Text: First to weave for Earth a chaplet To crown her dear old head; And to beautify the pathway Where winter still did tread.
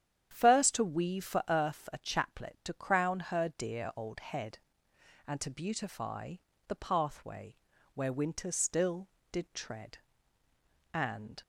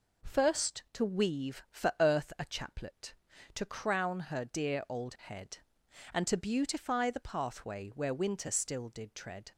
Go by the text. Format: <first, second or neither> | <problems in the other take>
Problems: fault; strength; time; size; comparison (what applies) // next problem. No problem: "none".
second | starts louder than the rest; strong; until 1.3 s; 9.5 dB // pauses between "beautify" and "the"; slight; at 6.3 s; 0.32 s long // pauses between "pathway" and "Where"; at 7.5 s; 0.38 s long // goes on to say "And"; slight; from 10.9 s on; 0.48 s long